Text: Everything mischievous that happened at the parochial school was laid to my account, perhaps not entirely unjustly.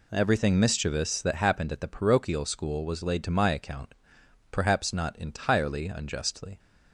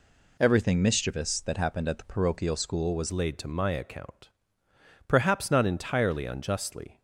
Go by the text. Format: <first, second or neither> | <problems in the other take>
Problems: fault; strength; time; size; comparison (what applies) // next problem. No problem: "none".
first | changes voice at "laid"; from 3.1 s on; 3.9 s long